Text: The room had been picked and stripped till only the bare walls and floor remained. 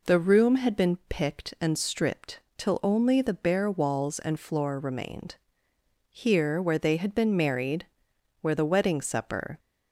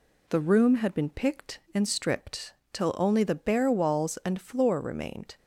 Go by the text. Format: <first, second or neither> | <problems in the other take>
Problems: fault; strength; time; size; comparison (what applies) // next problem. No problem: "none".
second | pauses between "stripped" and "till"; slight; at 2.4 s; 0.16 s long; slight in the second // goes on to say "Here where they had been married where the wedding supper"; strong; from 6.1 s on; 3.4 s long